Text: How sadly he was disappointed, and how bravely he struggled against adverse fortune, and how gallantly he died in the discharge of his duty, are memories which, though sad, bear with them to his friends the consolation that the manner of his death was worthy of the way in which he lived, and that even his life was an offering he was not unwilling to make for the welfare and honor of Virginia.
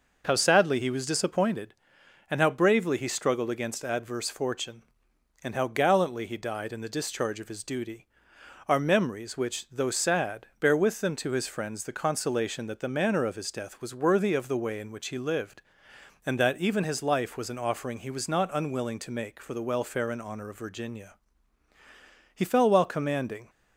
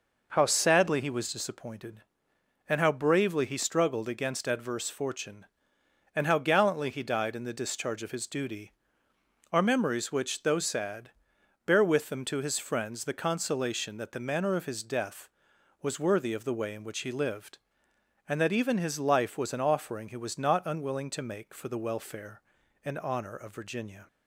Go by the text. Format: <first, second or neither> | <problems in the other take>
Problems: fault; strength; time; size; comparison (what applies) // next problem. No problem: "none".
second | goes on to say "He fell while commanding"; noticeable; from 22.3 s on; 1.1 s long